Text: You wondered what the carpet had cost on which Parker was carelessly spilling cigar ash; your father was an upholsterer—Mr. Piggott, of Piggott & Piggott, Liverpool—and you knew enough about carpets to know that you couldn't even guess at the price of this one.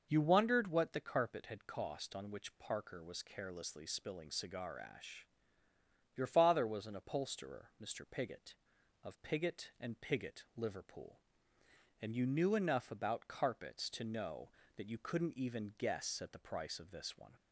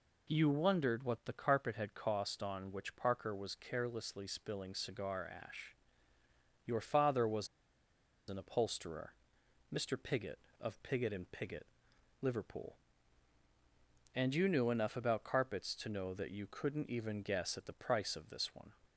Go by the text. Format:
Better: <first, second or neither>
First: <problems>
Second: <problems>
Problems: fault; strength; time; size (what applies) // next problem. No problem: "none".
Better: first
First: none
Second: pauses between "was" and "an"; noticeable; at 7.4 s; 0.81 s long